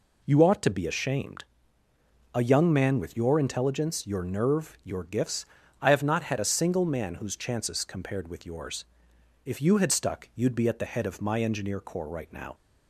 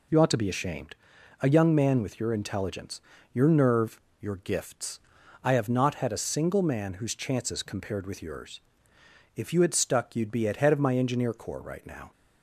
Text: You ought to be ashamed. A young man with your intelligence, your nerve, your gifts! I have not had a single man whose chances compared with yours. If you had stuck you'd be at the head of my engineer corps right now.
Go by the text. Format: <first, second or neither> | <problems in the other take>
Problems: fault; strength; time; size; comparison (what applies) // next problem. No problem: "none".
first | skips "the"; at 10.5 s